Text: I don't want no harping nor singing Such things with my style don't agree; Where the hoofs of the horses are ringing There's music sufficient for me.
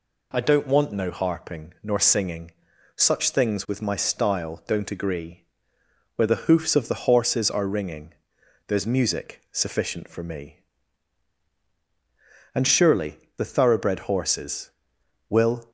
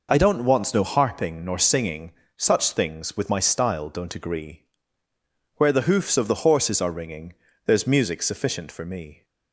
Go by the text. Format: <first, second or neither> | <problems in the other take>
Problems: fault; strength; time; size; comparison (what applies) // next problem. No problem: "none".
second | pauses between "singing" and "Such"; at 2.5 s; 0.44 s long; slight in the second // pauses between "ringing" and "There's"; noticeable; at 8.1 s; 0.52 s long; slight in the second // goes on to say "And surely the thoroughbred horses Will"; strong; from 12.5 s on; 3.1 s long